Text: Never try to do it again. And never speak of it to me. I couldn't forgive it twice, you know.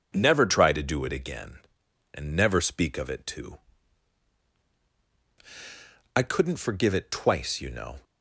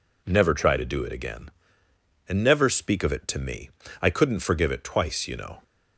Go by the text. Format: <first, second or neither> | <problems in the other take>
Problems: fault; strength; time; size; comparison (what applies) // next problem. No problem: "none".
second | skips "me"; at 4.8 s